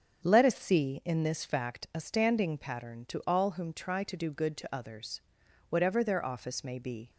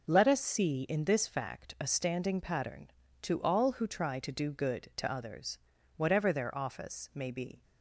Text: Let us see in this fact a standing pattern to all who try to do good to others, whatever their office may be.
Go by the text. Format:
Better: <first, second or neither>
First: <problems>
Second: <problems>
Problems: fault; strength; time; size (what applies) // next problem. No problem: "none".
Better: second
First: starts louder than the rest; until 1.2 s; 7 dB // says "whom" for "who"; at 3.5 s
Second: none